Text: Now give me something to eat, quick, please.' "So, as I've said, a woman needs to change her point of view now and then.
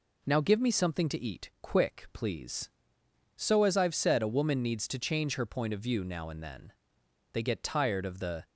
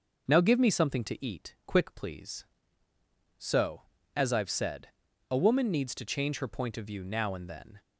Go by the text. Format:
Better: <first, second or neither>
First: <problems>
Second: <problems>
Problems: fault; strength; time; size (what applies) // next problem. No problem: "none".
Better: second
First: goes on to say "They get tired of the"; noticeable; from 7.3 s on; 1.1 s long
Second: none